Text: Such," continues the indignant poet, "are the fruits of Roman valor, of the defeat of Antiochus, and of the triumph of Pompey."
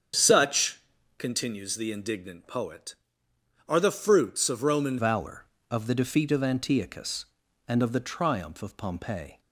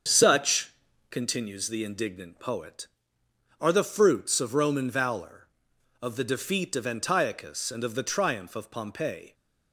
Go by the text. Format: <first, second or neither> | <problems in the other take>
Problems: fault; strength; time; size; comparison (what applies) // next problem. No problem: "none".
second | starts louder than the rest; strong; until 1.5 s; 7.5 dB; also in the second // changes voice at "valor"; from 4.9 s on; 4.4 s long